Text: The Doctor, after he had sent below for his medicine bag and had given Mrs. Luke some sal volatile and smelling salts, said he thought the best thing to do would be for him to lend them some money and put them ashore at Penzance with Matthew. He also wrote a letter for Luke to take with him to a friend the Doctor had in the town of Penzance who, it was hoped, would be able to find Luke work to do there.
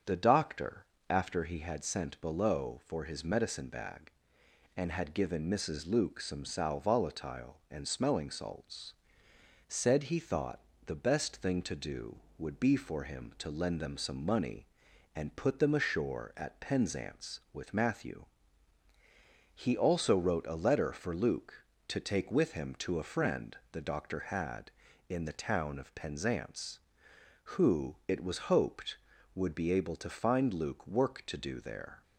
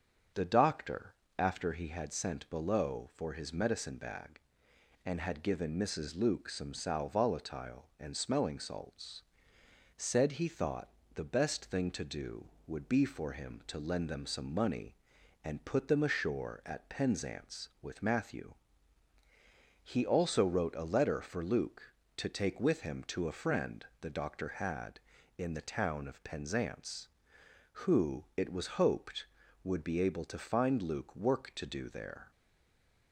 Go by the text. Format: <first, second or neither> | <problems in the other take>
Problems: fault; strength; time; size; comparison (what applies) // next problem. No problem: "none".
first | starts louder than the rest; strong; until 1.5 s; 7 dB; strong in the first // pauses between "thought" and "the"; slight; at 10.8 s; 0.26 s long; slight in the first // stays silent after the last word; slight; from 32.3 s on; 0.8 s long